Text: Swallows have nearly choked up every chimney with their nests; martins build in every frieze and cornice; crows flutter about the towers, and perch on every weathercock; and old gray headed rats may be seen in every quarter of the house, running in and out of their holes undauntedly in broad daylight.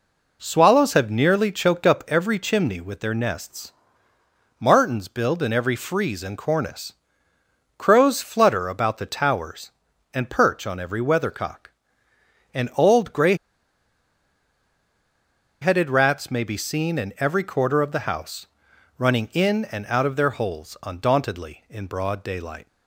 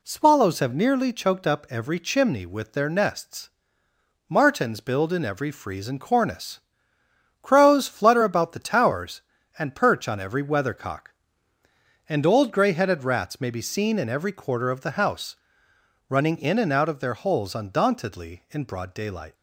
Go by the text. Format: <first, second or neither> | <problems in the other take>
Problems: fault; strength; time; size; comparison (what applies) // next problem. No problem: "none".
second | pauses between "gray" and "headed"; strong; at 13.3 s; 2.2 s long